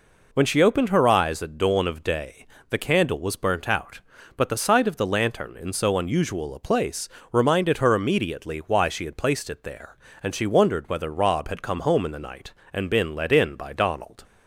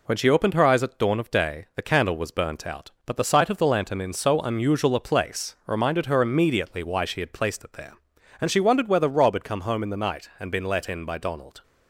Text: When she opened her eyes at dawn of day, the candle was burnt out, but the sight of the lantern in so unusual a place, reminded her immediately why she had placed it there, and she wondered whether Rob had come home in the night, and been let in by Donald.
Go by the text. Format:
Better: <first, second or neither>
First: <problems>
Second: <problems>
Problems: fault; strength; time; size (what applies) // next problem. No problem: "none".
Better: neither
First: none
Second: none